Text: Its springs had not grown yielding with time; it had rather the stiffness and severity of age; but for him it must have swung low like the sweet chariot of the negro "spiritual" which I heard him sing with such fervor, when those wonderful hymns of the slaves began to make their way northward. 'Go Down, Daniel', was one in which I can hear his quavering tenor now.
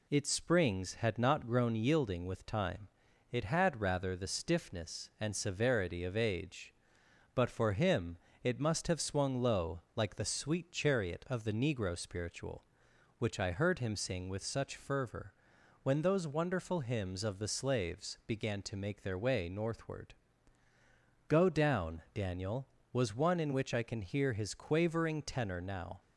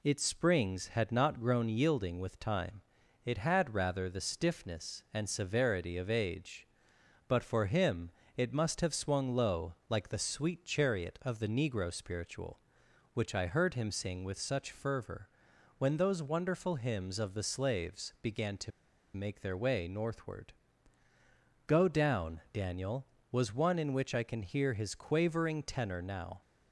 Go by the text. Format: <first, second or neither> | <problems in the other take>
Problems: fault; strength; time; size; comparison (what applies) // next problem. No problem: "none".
first | pauses between "him" and "it"; slight; at 8.1 s; 0.24 s long; slight in the first // pauses between "low" and "like"; slight; at 9.7 s; 0.16 s long; slight in the first // pauses between "to" and "make"; at 18.7 s; 0.44 s long